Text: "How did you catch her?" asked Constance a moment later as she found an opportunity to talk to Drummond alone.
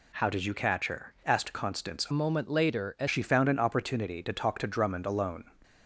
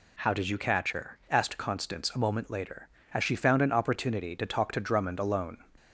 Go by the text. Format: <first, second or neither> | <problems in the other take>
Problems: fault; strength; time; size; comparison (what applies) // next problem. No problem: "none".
second | changes voice from "moment" to "as"; from 2.1 to 3.0 s; 0.9 s long